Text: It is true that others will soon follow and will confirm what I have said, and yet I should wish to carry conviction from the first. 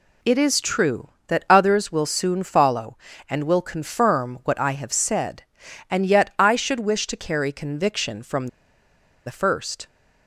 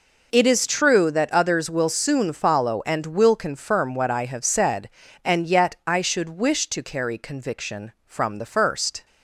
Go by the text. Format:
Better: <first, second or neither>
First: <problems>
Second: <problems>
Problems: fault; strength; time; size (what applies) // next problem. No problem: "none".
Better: second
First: pauses between "from" and "the"; noticeable; at 8.4 s; 0.78 s long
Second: none